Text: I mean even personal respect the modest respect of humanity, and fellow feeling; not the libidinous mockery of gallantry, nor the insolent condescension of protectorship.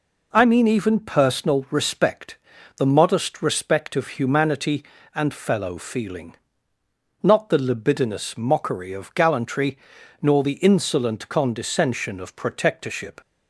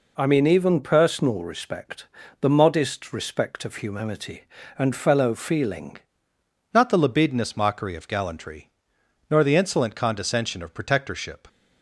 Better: first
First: pauses between "respect" and "the"; at 2.3 s; 0.40 s long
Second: pauses between "respect" and "the"; slight; at 2.0 s; 0.34 s long // changes voice at "not"; from 6.7 s on; 4.7 s long

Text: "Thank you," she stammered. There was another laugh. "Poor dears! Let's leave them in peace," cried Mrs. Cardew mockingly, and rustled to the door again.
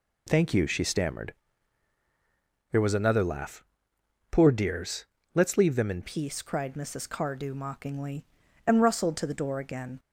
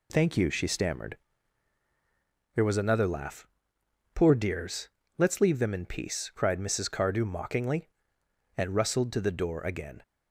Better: second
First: changes voice at "peace"; from 6.0 s on; 3.9 s long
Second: none

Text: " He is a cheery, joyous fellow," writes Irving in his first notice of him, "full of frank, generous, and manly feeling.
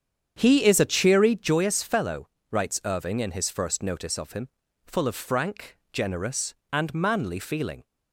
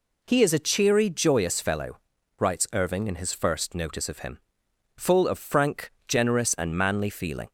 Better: second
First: starts louder than the rest; strong; until 1.6 s; 8 dB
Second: none

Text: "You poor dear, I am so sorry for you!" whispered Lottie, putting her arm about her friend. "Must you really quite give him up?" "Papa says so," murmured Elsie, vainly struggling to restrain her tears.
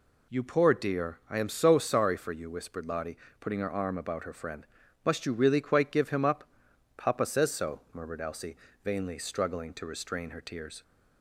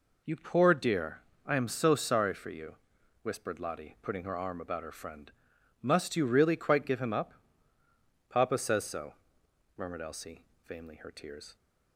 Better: first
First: none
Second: skips "struggling to restrain"; at 10.9 s

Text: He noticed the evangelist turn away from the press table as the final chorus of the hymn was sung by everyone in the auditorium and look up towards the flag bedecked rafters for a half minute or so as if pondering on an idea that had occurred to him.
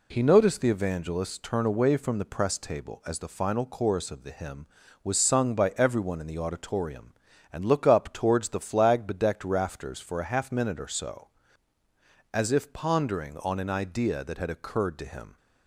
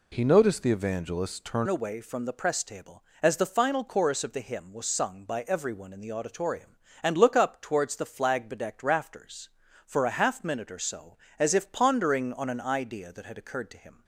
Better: first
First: none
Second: changes voice at "away"; from 1.6 s on; 12.4 s long

